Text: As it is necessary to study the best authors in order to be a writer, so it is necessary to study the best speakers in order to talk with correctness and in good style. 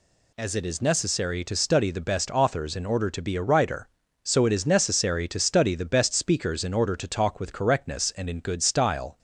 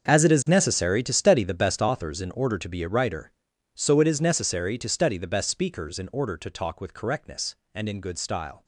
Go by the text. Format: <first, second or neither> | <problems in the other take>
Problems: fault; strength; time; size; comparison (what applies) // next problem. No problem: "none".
first | gets quieter; strong; throughout; 15 dB